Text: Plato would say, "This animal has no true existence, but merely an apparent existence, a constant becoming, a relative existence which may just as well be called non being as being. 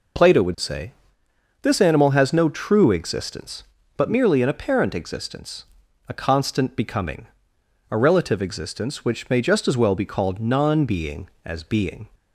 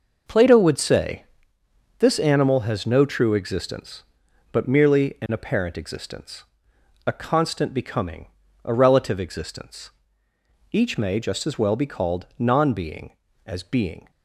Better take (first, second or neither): first